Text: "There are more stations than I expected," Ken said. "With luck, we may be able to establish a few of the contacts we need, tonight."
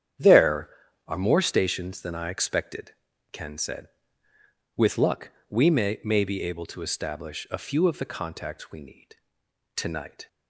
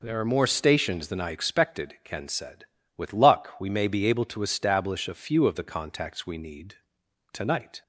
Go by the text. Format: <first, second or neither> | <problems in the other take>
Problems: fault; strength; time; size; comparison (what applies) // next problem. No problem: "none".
second | starts louder than the rest; strong; until 1.5 s; 9.5 dB // says "may" twice; at 6.0 s